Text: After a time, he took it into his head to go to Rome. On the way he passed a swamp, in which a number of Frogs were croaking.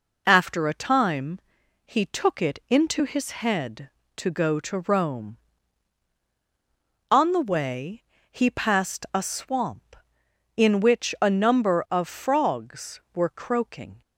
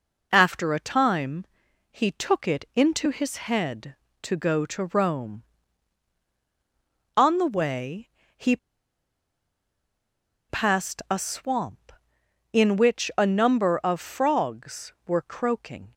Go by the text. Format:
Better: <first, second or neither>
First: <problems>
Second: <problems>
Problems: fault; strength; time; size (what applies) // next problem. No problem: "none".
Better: first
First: pauses between "way" and "he"; slight; at 8.0 s; 0.28 s long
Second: pauses between "way" and "he"; slight; at 8.0 s; 0.28 s long // pauses between "he" and "passed"; strong; at 8.5 s; 1.9 s long